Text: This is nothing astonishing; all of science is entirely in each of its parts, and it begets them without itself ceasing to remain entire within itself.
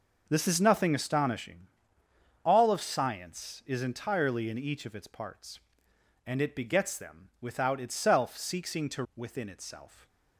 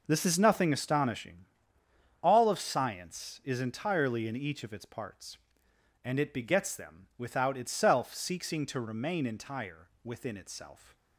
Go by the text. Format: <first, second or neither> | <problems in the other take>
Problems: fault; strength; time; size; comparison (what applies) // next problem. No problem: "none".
second | skips "remain entire"; at 9.0 s